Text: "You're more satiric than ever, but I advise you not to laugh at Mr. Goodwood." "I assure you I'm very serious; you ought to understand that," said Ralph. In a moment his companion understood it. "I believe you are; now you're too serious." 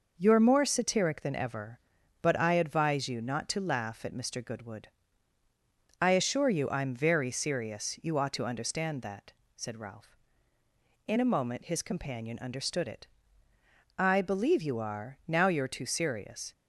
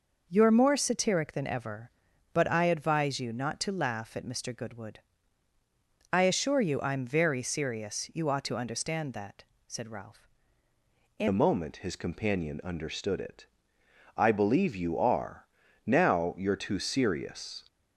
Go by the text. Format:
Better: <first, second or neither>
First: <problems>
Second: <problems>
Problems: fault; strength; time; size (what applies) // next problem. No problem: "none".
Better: first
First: none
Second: changes voice at "a"; from 11.2 s on; 6.4 s long